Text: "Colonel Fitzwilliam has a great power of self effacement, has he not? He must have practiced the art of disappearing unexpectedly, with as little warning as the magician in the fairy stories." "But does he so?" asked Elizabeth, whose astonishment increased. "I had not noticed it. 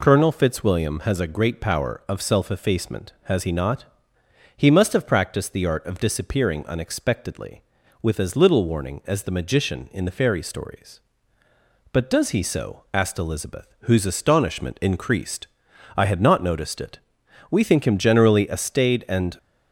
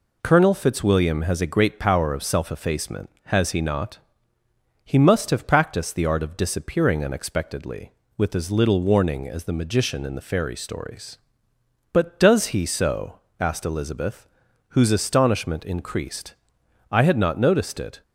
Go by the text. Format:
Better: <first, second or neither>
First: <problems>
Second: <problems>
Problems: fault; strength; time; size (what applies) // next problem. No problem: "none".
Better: second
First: goes on to say "We think him generally a staid and"; strong; from 17.5 s on; 1.8 s long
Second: none